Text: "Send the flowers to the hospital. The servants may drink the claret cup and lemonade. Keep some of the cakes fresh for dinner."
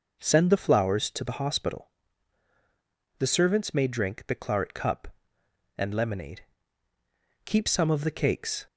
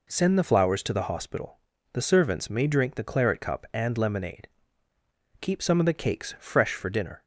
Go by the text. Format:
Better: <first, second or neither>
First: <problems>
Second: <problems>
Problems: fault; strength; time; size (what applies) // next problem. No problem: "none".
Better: second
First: stops before "fresh for dinner"; at 8.6 s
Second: none